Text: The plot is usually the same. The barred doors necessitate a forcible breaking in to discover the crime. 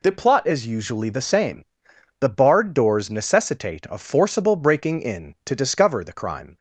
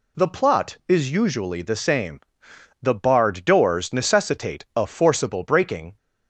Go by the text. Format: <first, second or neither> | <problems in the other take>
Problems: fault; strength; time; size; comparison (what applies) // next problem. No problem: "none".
first | stops before "in to discover the crime"; at 5.9 s